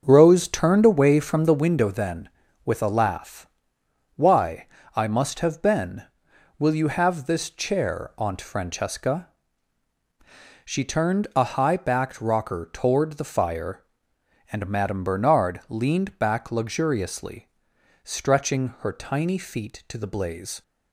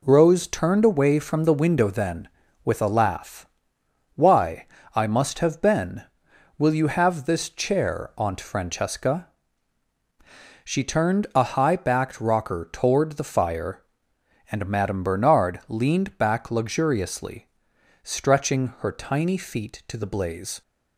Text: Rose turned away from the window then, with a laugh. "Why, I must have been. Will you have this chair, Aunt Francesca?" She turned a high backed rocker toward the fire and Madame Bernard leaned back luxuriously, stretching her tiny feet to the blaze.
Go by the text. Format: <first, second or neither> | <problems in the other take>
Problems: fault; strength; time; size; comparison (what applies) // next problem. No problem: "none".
second | starts louder than the rest; until 1.7 s; 6.5 dB